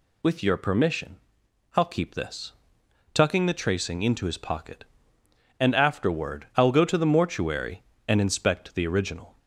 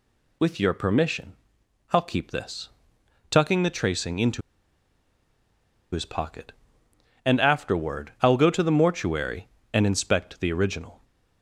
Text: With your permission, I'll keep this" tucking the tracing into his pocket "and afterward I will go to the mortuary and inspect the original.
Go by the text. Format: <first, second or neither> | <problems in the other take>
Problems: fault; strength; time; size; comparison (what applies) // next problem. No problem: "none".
first | pauses between "this" and "tucking"; noticeable; at 2.6 s; 0.62 s long; noticeable in the first // pauses between "into" and "his"; strong; at 4.4 s; 1.5 s long